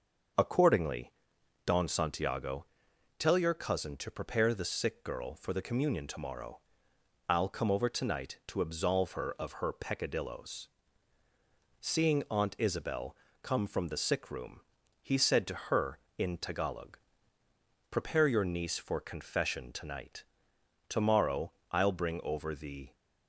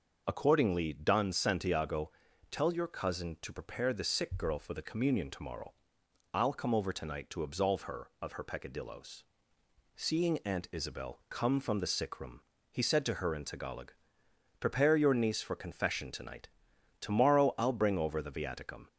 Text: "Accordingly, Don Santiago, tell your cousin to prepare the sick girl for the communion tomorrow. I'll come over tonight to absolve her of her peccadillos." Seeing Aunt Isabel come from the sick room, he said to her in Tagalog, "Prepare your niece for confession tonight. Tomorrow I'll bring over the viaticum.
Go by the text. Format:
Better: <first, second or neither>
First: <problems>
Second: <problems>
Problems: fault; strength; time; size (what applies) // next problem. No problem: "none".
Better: second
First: starts louder than the rest; until 1.8 s; 6.5 dB // pauses between "Isabel" and "come"; slight; at 13.1 s; 0.26 s long // pauses between "Tomorrow" and "I'll"; slight; at 21.5 s; 0.18 s long // stops before "viaticum"; at 22.9 s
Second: none